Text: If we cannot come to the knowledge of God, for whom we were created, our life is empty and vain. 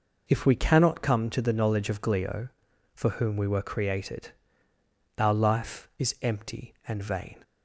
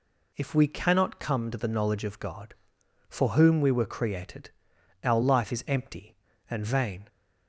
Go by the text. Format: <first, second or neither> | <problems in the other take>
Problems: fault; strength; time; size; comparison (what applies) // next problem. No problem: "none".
second | says "Glio" for "God"; at 2.0 s